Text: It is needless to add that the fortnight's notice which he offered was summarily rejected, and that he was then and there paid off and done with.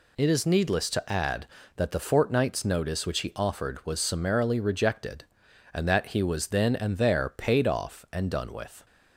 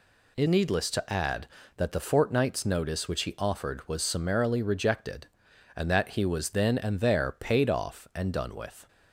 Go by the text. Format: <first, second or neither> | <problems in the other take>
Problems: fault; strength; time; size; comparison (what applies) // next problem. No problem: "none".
first | skips "is"; at 0.4 s